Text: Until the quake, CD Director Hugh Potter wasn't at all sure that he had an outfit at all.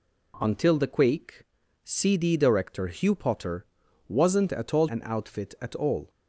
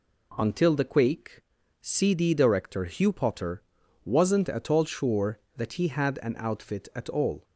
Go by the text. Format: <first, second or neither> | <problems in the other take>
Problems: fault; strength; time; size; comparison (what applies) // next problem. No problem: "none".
second | pauses between "Potter" and "wasn't"; at 3.6 s; 0.44 s long; also in the second // skips "sure that he had"; at 4.8 s